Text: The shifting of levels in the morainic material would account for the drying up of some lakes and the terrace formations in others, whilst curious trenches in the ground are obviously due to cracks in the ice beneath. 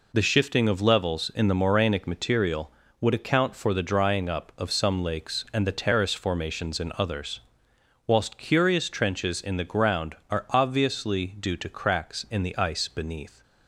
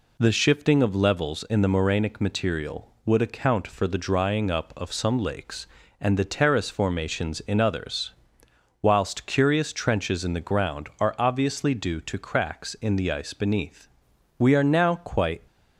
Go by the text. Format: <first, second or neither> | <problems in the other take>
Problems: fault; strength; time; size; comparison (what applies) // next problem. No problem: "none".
first | goes on to say "We are now quite"; noticeable; from 14.3 s on; 1.0 s long